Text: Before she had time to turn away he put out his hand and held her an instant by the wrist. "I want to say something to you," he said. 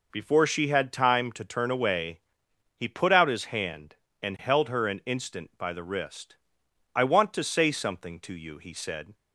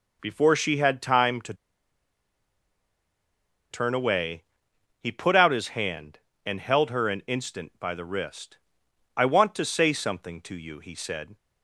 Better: first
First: pauses between "away" and "he"; noticeable; at 2.2 s; 0.56 s long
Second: pauses between "to" and "turn"; strong; at 1.5 s; 2.1 s long // pauses between "away" and "he"; noticeable; at 4.4 s; 0.56 s long

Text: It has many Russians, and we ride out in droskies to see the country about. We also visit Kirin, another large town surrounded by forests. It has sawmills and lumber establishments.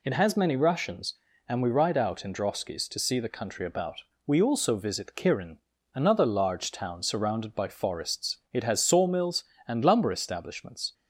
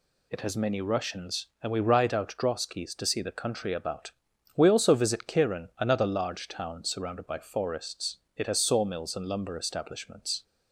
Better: first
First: none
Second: skips "in"; at 2.3 s

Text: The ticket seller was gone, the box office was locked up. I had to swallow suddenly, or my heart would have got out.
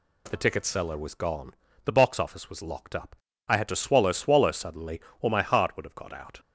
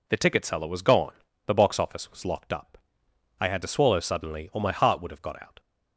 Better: second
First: says "swallow" twice; at 4.1 s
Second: none

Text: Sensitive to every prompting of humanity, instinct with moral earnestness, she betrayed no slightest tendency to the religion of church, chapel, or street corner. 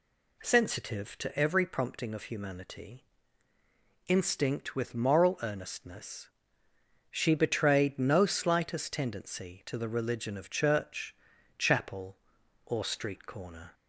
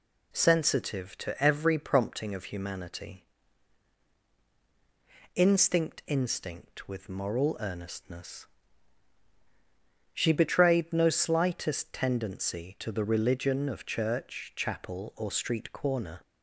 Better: first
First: none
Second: says "instinct" twice; at 6.0 s

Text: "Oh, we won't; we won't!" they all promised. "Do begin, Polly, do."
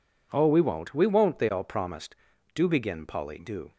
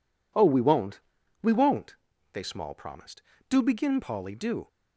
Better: first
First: none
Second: says "small" for "all"; at 2.4 s

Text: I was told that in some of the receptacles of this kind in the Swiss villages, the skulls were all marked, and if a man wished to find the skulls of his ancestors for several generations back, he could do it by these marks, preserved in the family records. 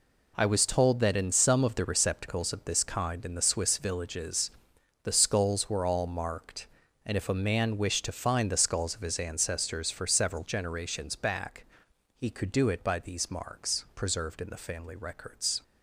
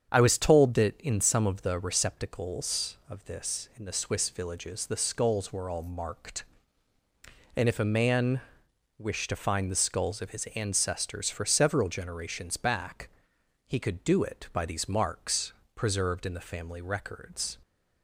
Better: first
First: none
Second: starts louder than the rest; strong; until 1.1 s; 7.5 dB // skips "kind"; at 3.7 s // pauses between "man" and "wished"; noticeable; at 8.4 s; 0.56 s long

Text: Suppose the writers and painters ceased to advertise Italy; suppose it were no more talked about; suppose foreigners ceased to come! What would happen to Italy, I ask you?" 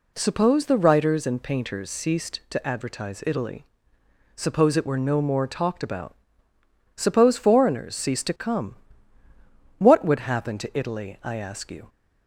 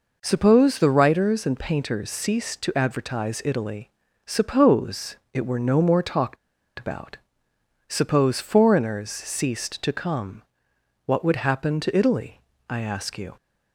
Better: first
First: none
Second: pauses between "suppose" and "it"; slight; at 5.1 s; 0.16 s long // pauses between "talked" and "about"; at 6.3 s; 0.42 s long

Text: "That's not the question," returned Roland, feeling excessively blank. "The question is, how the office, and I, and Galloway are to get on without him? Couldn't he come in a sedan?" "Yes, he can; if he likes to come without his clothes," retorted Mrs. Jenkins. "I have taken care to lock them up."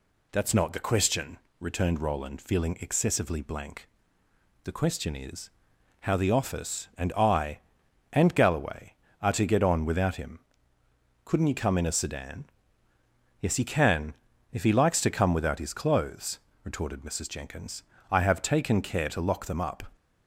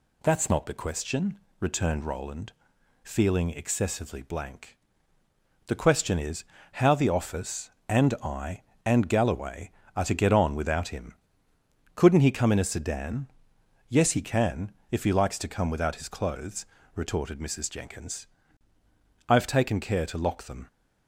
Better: first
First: none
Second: stops before "up"; at 20.6 s

